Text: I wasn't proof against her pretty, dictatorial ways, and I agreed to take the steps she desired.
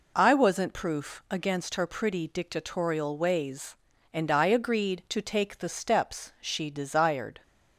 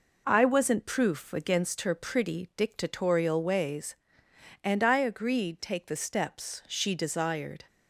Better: first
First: none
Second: skips "to"; at 5.6 s

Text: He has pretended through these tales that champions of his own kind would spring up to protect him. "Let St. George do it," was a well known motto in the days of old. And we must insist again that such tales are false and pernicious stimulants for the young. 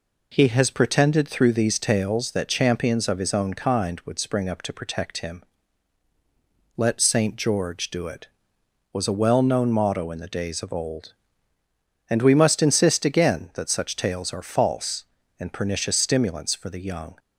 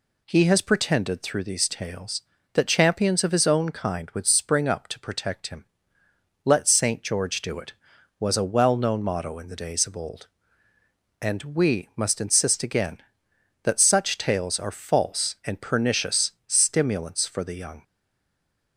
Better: first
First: none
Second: pauses between "pernicious" and "stimulants"; slight; at 16.3 s; 0.16 s long // stays silent after the last word; slight; from 17.8 s on; 0.9 s long

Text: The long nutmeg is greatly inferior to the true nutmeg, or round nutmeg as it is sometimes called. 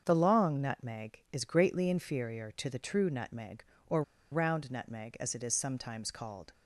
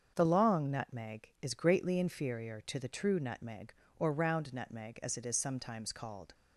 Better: second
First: starts louder than the rest; until 1.0 s; 7 dB // pauses between "or" and "round"; slight; at 4.0 s; 0.30 s long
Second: starts louder than the rest; strong; until 1.1 s; 7 dB

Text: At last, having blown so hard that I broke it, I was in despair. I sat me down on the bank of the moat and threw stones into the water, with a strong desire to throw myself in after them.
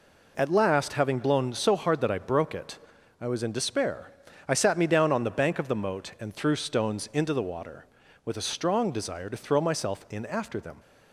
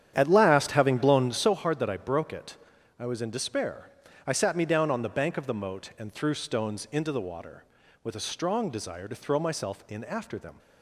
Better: first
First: none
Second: starts louder than the rest; strong; until 1.6 s; 9.5 dB

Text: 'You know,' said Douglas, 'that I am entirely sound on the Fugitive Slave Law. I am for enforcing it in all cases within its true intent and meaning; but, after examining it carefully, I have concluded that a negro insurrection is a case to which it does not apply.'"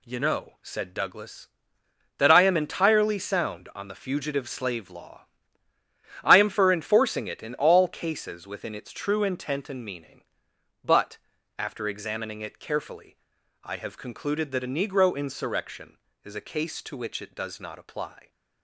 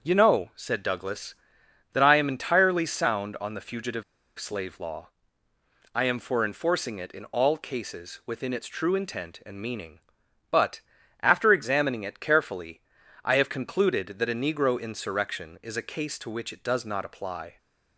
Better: first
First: none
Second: starts louder than the rest; until 1.0 s; 6.5 dB // pauses between "Fugitive" and "Slave"; slight; at 4.0 s; 0.35 s long

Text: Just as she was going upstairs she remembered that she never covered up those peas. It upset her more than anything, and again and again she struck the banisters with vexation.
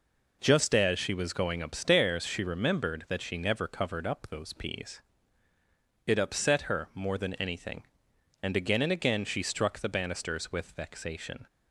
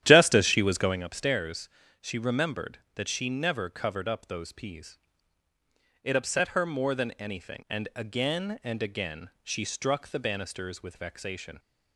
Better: first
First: none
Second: starts louder than the rest; strong; until 1.1 s; 11.5 dB // pauses between "upstairs" and "she"; slight; at 1.6 s; 0.34 s long

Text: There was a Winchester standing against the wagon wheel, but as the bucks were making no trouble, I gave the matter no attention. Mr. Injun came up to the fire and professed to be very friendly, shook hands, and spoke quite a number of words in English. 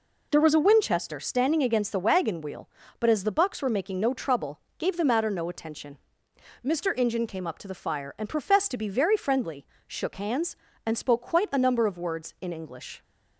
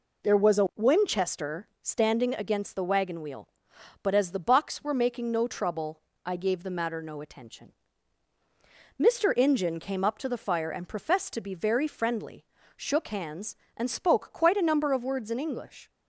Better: second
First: skips "I"; at 4.6 s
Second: none

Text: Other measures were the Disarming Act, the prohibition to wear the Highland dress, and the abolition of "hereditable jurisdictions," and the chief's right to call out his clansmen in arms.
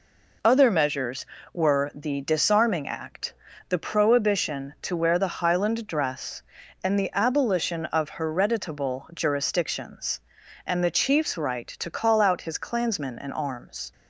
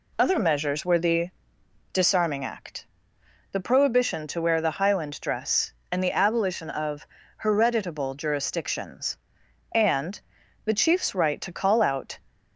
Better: first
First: none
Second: pauses between "the" and "Disarming"; noticeable; at 1.3 s; 0.60 s long // pauses between "of" and "hereditable"; slight; at 7.0 s; 0.34 s long // pauses between "and" and "the"; noticeable; at 10.1 s; 0.46 s long // stops before "his clansmen in arms"; at 12.2 s

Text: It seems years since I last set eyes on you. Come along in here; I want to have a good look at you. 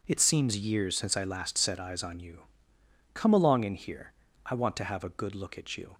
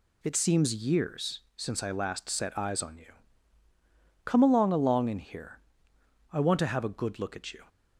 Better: first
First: none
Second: pauses between "years" and "since"; slight; at 1.3 s; 0.16 s long // says "along" twice; at 4.7 s

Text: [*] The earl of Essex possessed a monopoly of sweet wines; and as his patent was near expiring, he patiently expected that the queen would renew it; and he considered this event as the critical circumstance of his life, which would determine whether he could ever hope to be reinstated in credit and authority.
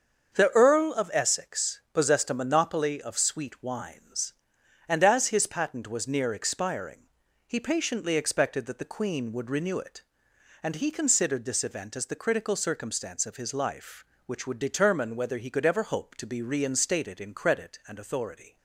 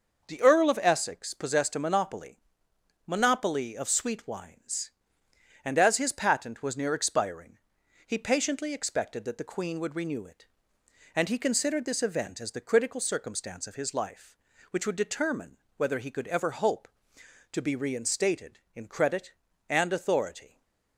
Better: first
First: starts louder than the rest; until 1.4 s; 7 dB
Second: starts louder than the rest; noticeable; until 1.2 s; 6 dB // says "monopoly" twice; at 3.0 s // pauses between "determine" and "whether"; slight; at 15.5 s; 0.18 s long // stays silent after the last word; slight; from 20.4 s on; 0.5 s long

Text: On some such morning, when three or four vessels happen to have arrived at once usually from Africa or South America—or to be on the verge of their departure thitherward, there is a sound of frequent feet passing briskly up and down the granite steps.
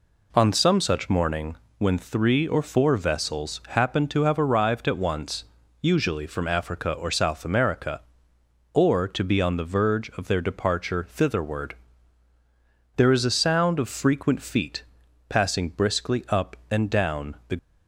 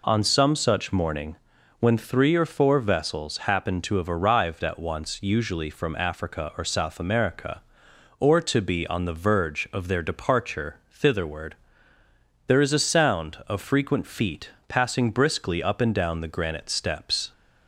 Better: second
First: pauses between "once" and "usually"; slight; at 5.4 s; 0.36 s long // pauses between "feet" and "passing"; noticeable; at 14.8 s; 0.46 s long // stops before "granite steps"; at 17.5 s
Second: pauses between "feet" and "passing"; slight; at 14.5 s; 0.18 s long

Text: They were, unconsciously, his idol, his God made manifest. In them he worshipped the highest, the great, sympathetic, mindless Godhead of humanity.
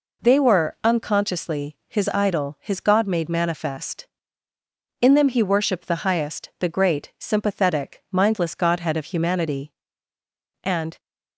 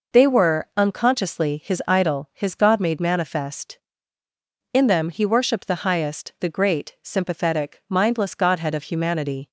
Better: second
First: goes on to say "And"; slight; from 10.6 s on; 0.36 s long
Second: none

